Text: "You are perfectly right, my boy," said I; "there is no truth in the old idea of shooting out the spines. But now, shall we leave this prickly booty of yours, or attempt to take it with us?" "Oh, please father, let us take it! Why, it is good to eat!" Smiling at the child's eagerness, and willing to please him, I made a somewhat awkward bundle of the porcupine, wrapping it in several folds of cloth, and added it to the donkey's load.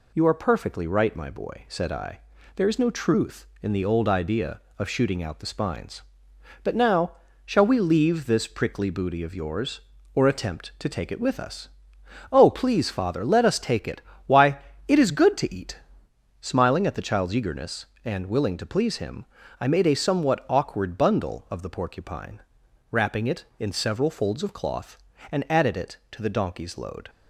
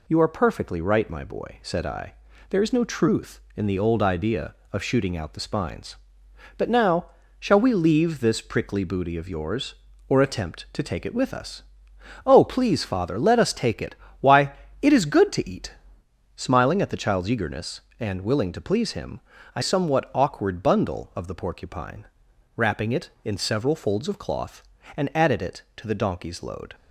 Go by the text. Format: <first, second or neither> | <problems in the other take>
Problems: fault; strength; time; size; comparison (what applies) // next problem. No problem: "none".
first | skips "made a"; at 19.6 s